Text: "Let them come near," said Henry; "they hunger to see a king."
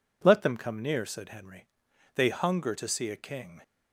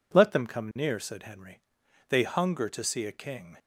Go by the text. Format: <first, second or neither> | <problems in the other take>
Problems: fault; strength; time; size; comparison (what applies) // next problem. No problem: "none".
neither | none